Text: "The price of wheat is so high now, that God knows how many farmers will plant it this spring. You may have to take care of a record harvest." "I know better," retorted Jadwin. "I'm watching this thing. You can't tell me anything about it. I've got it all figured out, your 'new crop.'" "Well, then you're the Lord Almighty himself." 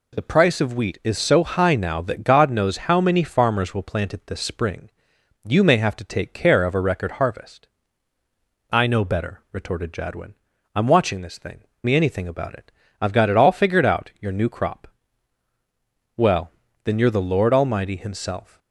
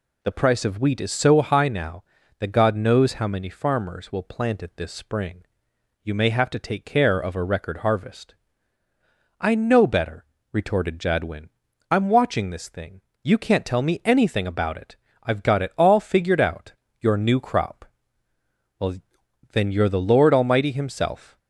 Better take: second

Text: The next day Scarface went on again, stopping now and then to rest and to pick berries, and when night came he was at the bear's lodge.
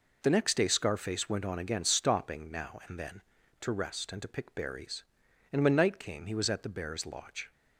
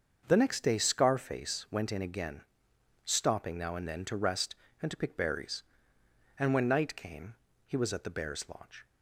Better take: first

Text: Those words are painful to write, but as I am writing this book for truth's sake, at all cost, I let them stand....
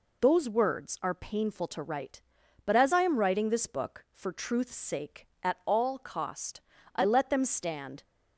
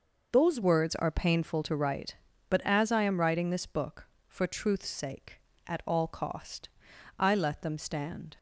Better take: first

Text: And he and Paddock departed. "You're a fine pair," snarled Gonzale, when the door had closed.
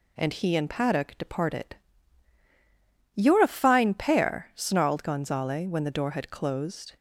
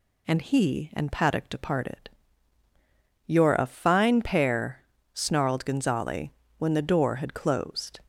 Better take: neither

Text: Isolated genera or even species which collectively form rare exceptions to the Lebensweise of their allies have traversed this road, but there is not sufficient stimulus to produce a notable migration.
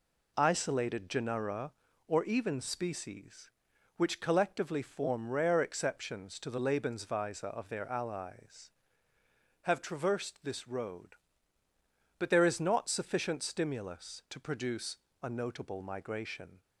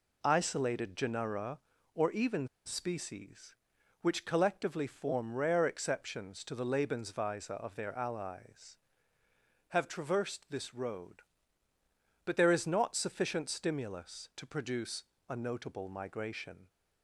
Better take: first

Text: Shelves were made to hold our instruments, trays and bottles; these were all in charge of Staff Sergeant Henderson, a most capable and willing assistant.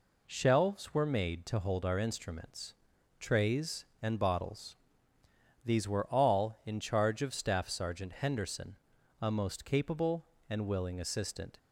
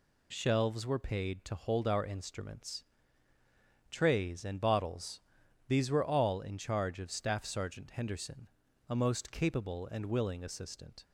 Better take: first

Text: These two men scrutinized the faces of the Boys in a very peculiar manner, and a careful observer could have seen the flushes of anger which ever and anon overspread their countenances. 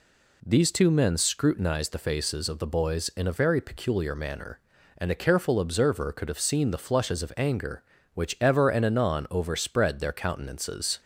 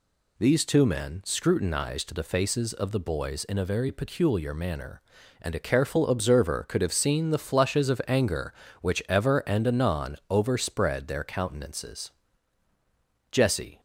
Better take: first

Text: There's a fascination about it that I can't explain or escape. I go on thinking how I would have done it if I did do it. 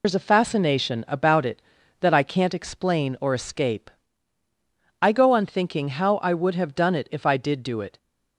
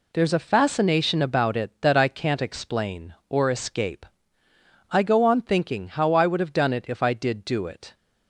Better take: second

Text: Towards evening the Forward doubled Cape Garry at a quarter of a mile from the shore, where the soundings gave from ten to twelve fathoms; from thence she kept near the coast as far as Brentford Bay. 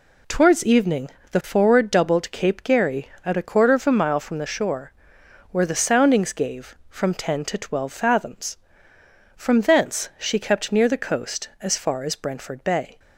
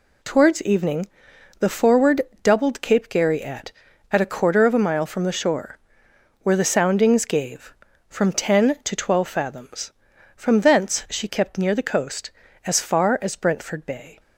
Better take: first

